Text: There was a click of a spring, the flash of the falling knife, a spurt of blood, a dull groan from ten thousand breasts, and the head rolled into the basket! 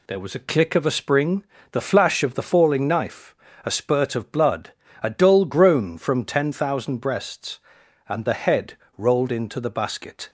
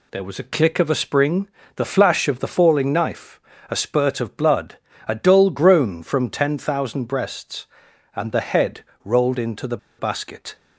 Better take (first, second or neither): first